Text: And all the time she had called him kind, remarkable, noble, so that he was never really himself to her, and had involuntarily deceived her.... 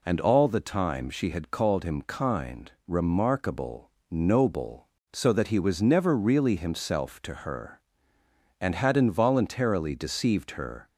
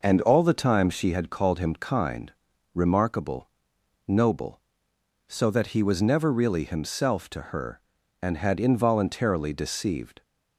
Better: first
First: none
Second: stops before "her"; at 10.2 s

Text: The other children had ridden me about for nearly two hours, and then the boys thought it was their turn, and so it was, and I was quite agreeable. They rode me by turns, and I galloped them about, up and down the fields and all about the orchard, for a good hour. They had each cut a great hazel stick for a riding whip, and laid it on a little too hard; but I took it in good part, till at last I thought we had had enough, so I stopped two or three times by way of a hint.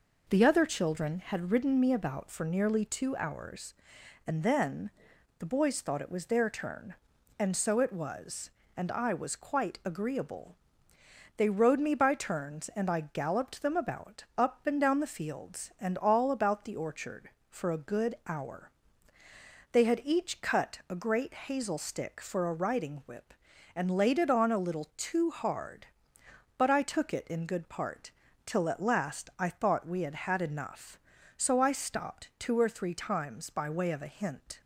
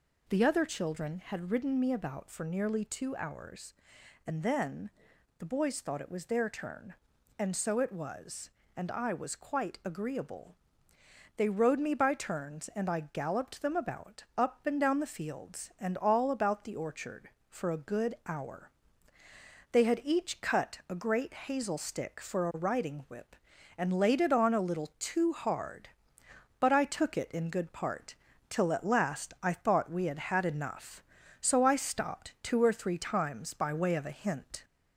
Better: first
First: pauses between "then" and "the"; noticeable; at 4.8 s; 0.48 s long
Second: gets louder; slight; throughout; 2 dB // pauses between "then" and "the"; noticeable; at 4.8 s; 0.48 s long

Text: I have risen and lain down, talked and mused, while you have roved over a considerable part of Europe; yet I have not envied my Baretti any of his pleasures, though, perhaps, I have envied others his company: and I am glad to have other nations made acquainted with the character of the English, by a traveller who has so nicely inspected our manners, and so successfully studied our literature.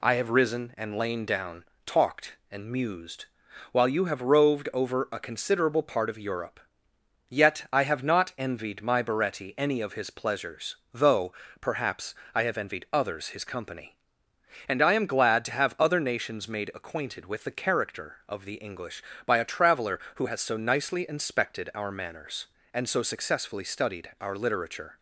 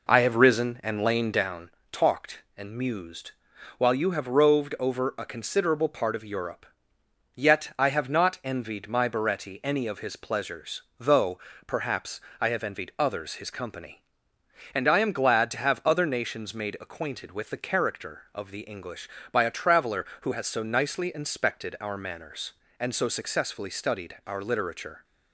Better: first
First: none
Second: starts louder than the rest; noticeable; until 1.6 s; 4.5 dB

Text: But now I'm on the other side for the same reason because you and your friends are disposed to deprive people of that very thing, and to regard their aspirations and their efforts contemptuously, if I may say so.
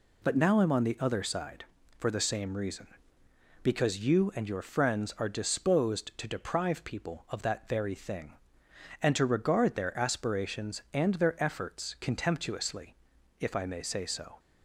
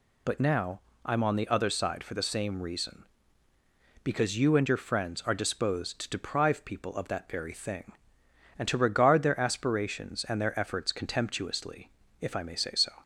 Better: first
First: none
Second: loses the start of "But"; at 0.2 s; 65 ms // pauses between "now" and "I'm"; slight; at 0.8 s; 0.24 s long

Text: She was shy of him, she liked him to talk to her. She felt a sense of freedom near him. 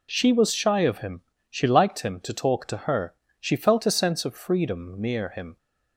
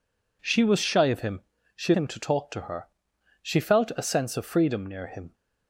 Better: first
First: none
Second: skips "liked"; at 1.9 s

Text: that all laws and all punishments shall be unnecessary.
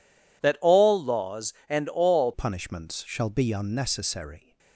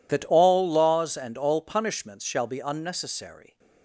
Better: second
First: changes voice at "punishments"; from 2.3 s on; 2.2 s long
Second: none

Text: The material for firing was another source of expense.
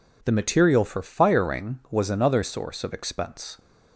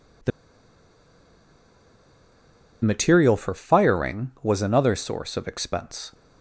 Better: first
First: none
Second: pauses between "The" and "material"; strong; at 0.3 s; 2.5 s long

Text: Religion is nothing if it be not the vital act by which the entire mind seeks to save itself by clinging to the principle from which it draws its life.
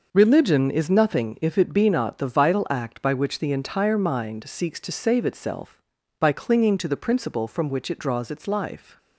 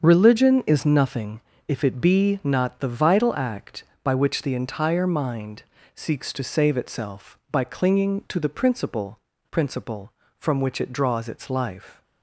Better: first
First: none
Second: starts louder than the rest; until 1.0 s; 7 dB // pauses between "nothing" and "if"; slight; at 1.4 s; 0.28 s long // pauses between "mind" and "seeks"; slight; at 5.6 s; 0.34 s long // says "principle" twice; at 9.5 s

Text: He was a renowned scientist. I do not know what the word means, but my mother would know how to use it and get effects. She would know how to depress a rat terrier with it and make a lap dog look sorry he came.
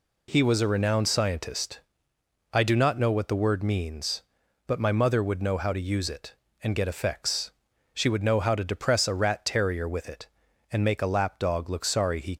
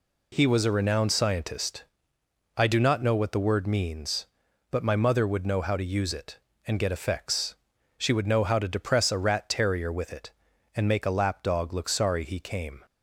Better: second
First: stops before "came"; at 12.3 s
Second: none

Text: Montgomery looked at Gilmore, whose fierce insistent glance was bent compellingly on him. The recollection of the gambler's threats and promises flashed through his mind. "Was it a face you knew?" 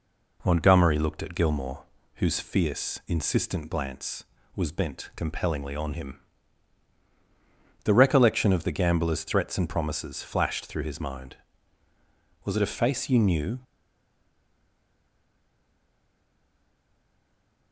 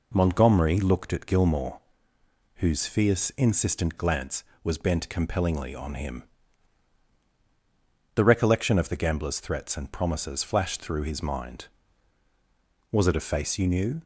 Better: second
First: stays silent after the last word; strong; from 13.6 s on; 4.1 s long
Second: none

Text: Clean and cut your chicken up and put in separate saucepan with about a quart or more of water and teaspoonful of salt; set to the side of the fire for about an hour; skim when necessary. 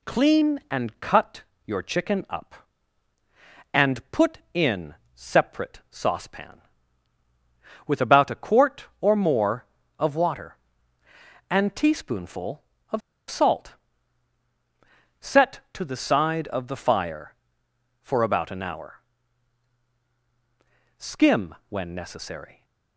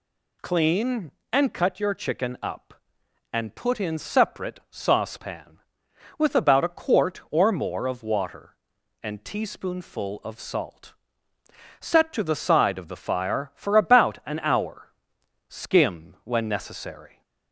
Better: second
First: pauses between "cut" and "your"; slight; at 1.4 s; 0.22 s long // pauses between "in" and "separate"; slight; at 4.9 s; 0.20 s long // pauses between "of" and "salt"; slight; at 13.0 s; 0.29 s long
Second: none

